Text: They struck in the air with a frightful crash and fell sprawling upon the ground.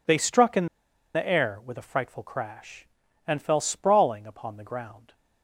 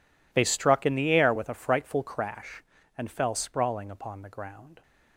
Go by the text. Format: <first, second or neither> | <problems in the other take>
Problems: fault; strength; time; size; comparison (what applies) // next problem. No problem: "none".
second | pauses between "in" and "the"; noticeable; at 0.6 s; 0.48 s long